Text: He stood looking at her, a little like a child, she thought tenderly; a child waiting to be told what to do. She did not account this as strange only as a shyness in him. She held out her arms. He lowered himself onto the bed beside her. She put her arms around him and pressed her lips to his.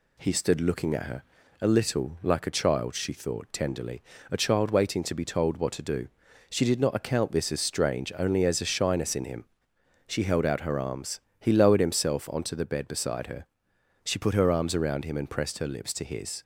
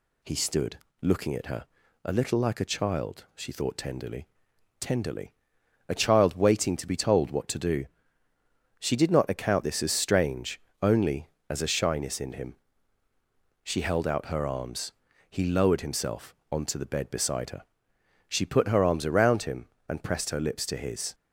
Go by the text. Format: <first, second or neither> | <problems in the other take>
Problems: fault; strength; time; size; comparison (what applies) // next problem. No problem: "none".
first | pauses between "stood" and "looking"; slight; at 0.7 s; 0.22 s long // says "tenderly" twice; at 4.7 s // pauses between "strange" and "only"; slight; at 10.6 s; 0.22 s long // pauses between "himself" and "onto"; slight; at 16.3 s; 0.16 s long